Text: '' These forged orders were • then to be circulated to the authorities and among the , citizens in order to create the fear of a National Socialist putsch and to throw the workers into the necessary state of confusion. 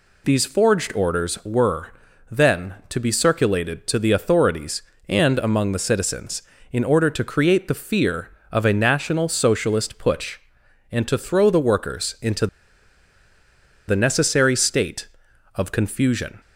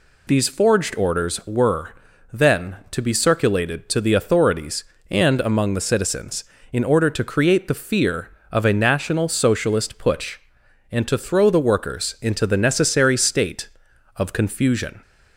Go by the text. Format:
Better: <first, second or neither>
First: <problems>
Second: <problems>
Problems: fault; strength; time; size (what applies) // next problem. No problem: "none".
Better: second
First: pauses between "into" and "the"; strong; at 12.4 s; 1.4 s long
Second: none